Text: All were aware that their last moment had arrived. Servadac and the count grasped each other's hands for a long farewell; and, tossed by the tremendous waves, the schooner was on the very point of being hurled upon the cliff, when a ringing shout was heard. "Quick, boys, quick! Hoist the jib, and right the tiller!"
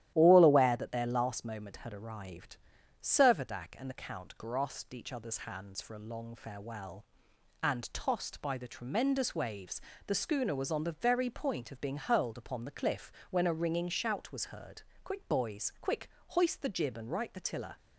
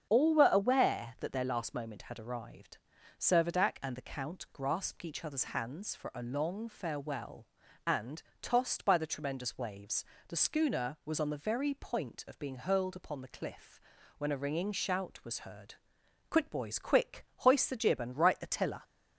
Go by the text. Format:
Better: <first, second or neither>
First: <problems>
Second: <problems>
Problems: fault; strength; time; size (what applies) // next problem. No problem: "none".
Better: second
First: starts louder than the rest; strong; until 1.1 s; 12.5 dB // skips "were"; at 0.4 s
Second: starts louder than the rest; strong; until 1.1 s; 7.5 dB